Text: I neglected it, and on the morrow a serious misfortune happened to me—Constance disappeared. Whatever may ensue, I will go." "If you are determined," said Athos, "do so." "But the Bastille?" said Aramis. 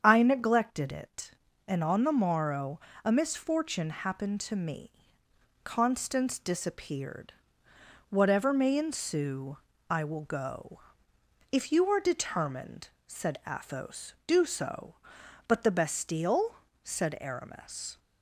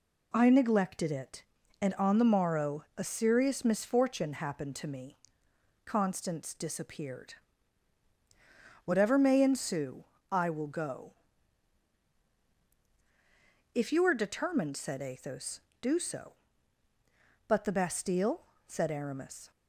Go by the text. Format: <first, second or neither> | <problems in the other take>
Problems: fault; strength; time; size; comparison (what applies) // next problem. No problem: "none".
second | starts louder than the rest; strong; until 1.0 s; 8 dB // pauses between "morrow" and "a"; slight; at 2.7 s; 0.26 s long // skips "serious"; at 3.1 s